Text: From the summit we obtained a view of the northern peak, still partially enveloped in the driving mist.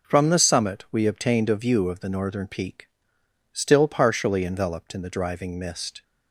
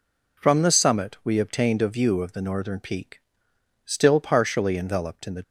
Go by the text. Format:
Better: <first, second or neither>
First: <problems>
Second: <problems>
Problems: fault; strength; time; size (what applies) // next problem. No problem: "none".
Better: first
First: none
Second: stops before "driving mist"; at 5.4 s